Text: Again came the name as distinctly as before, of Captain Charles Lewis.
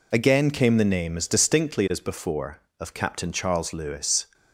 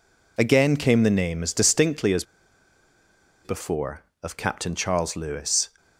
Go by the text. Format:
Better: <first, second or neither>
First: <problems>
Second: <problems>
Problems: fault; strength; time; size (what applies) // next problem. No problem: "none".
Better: first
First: none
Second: pauses between "as" and "before"; at 2.2 s; 1.2 s long